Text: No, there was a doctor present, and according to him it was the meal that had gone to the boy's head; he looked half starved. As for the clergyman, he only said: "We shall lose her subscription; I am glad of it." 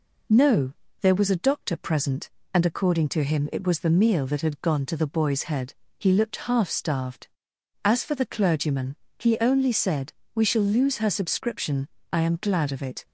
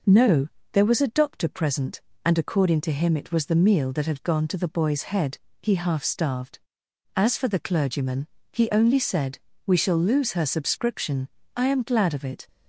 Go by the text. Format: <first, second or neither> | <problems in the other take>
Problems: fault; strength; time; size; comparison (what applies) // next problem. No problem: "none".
first | skips "looked"; at 5.7 s